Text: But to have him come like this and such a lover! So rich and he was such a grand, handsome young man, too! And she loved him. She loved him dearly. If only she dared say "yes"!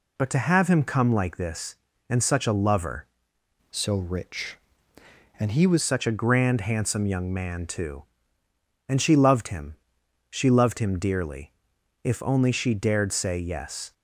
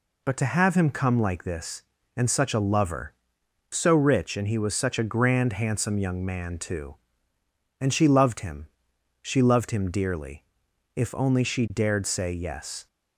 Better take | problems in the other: second | changes voice from "So" to "was"; from 3.6 to 5.8 s; 2.2 s long

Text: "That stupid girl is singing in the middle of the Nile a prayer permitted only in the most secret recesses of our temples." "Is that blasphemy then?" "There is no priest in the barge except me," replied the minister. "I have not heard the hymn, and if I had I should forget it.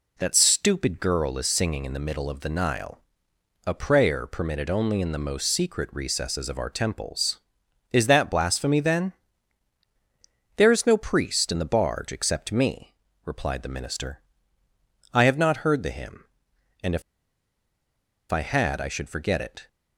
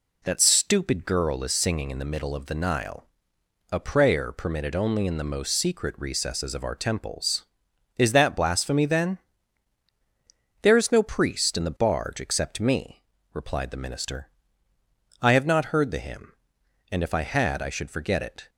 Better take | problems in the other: second | pauses between "Nile" and "a"; noticeable; at 3.0 s; 0.66 s long; noticeable in the second // pauses between "if" and "I"; strong; at 17.0 s; 1.2 s long

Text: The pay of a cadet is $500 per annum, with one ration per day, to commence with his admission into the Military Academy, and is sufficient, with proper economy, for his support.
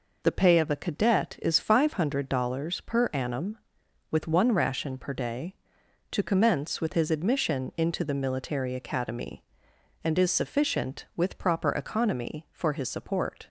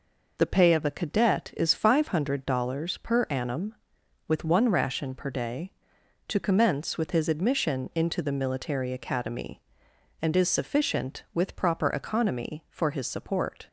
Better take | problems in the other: neither | none

